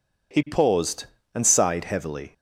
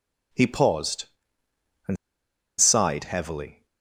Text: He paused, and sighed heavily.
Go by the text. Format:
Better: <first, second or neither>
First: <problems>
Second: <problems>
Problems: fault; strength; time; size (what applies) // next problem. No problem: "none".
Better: first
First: none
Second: pauses between "and" and "sighed"; noticeable; at 1.9 s; 0.64 s long